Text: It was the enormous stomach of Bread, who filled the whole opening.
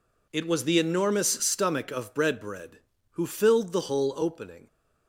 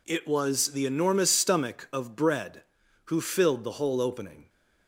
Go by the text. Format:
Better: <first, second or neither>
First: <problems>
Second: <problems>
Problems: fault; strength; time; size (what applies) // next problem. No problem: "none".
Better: second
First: says "Bread" twice; at 2.4 s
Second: none